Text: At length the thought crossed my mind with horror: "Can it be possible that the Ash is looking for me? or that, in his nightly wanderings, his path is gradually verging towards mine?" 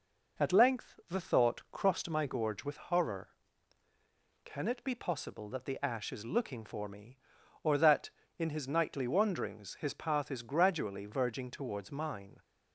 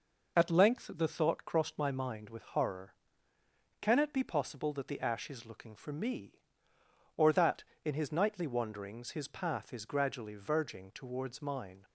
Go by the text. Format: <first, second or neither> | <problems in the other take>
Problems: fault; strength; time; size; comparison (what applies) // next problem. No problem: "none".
second | says "gorge" for "mind"; at 2.2 s